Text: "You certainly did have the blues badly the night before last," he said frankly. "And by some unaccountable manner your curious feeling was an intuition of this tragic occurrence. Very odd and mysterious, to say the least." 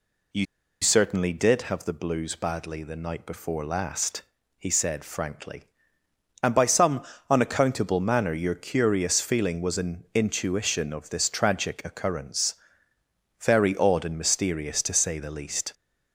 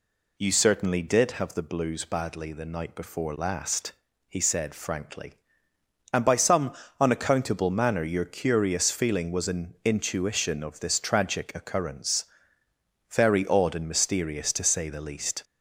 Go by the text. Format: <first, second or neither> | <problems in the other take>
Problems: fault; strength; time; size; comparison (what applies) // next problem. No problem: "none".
second | pauses between "You" and "certainly"; at 0.4 s; 0.36 s long // pauses between "some" and "unaccountable"; slight; at 7.0 s; 0.26 s long; slight in the second